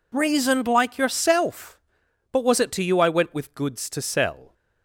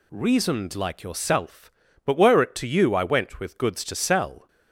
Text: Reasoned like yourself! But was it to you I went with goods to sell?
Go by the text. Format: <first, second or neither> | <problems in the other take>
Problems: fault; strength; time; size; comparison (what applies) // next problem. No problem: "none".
first | says "were" for "was"; at 2.1 s